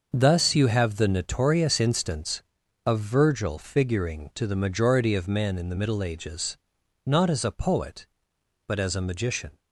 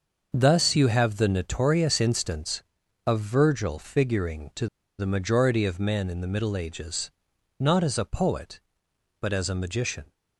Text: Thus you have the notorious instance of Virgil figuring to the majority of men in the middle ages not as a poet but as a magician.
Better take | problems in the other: first | starts louder than the rest; until 1.3 s; 6 dB; also in the first // pauses between "to" and "the"; slight; at 4.6 s; 0.32 s long // pauses between "ages" and "not"; noticeable; at 7.1 s; 0.48 s long; noticeable in the first

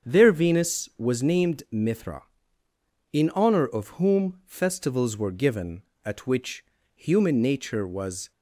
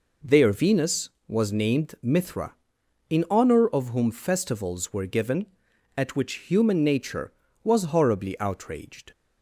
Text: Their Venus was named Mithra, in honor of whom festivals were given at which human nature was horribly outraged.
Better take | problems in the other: second | starts louder than the rest; strong; until 1.1 s; 7.5 dB // pauses between "which" and "human"; slight; at 6.6 s; 0.30 s long // stops before "horribly outraged"; at 8.3 s

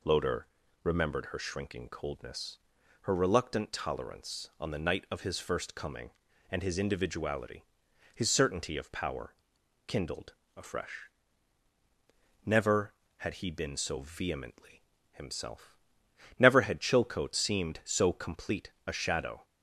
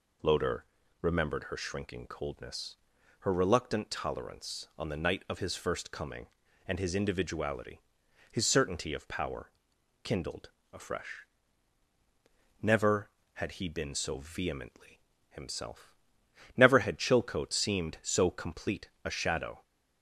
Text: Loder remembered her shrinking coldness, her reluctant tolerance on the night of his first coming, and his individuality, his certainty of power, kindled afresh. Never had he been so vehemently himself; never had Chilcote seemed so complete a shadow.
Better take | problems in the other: neither | pauses between "Loder" and "remembered"; slight; the same in both // pauses between "kindled" and "afresh"; slight; the same in both // pauses between "vehemently" and "himself"; slight; the same in both

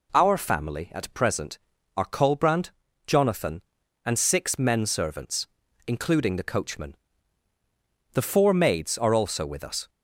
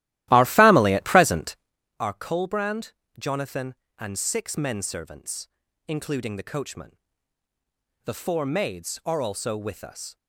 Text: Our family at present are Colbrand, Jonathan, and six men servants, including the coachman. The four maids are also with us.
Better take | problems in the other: first | starts louder than the rest; strong; until 1.8 s; 15.5 dB

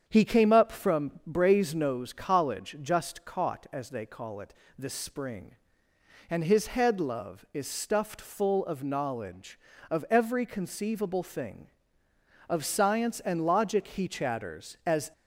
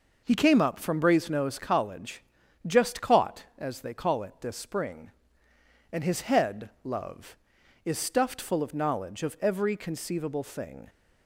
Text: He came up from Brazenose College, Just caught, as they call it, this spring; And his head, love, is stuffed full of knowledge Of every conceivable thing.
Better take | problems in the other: second | starts louder than the rest; strong; until 1.0 s; 8 dB // goes on to say "Of science and logic he chatters As"; strong; from 12.4 s on; 2.6 s long

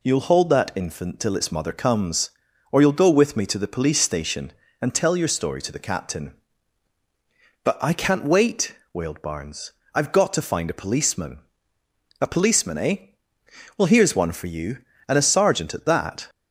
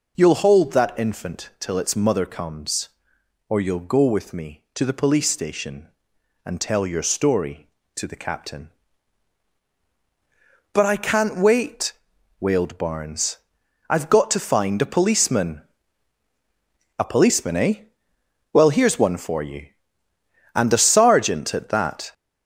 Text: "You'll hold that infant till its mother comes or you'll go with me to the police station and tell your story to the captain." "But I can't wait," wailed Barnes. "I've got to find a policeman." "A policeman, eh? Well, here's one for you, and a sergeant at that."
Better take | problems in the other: first | gets louder; noticeable; throughout; 6 dB

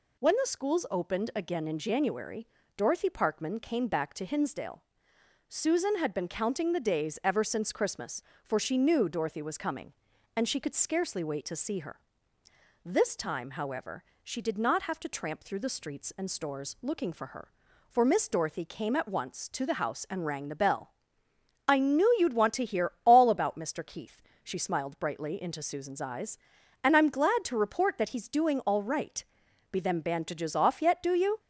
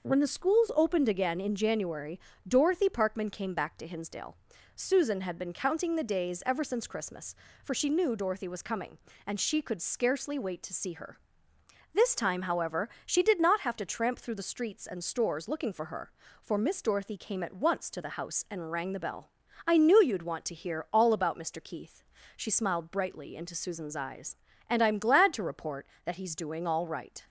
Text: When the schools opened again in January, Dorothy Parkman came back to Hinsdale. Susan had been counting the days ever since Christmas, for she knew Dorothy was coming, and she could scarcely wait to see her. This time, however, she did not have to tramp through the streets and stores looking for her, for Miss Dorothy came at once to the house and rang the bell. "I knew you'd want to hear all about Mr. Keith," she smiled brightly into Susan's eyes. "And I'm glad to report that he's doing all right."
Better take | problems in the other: second | goes on to say "Be them bandages off yet Do you"; strong; from 29.7 s on; 1.6 s long

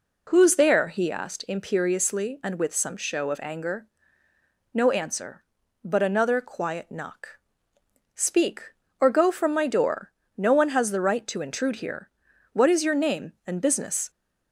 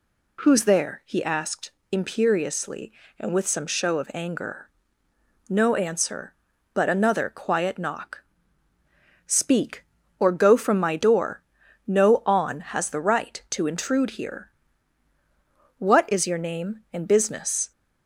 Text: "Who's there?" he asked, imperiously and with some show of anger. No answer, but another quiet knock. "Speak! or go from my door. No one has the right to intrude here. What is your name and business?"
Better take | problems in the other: first | says "on" for "one"; at 12.2 s

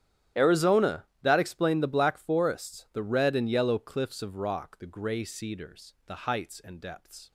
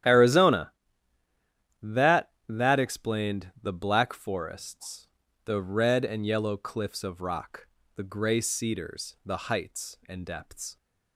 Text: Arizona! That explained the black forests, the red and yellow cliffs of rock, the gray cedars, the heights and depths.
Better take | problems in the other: first | starts louder than the rest; strong; until 2.1 s; 11.5 dB; strong in the first // says "That" twice; at 2.4 s

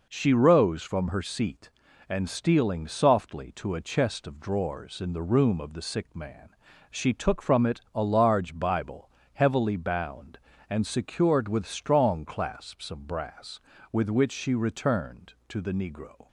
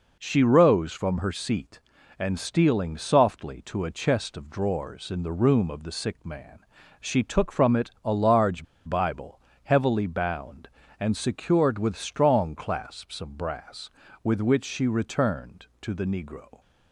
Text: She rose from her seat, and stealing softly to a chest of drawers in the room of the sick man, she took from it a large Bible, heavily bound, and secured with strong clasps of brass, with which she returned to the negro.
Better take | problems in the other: first | pauses between "large" and "Bible"; slight; at 8.6 s; 0.22 s long

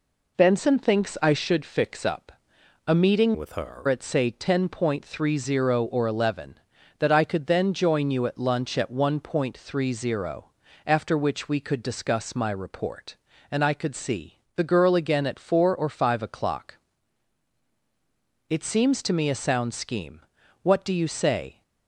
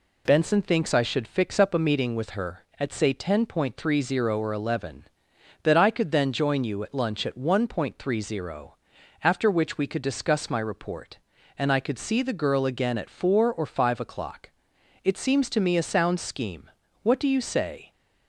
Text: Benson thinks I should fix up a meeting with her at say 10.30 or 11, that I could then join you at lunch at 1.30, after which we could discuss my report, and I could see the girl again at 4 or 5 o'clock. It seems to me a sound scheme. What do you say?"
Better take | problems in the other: second | pauses between "up" and "a"; noticeable; at 2.3 s; 0.54 s long // changes voice from "with" to "her"; from 3.3 to 3.8 s; 0.5 s long // pauses between "see" and "the"; slight; at 14.3 s; 0.16 s long

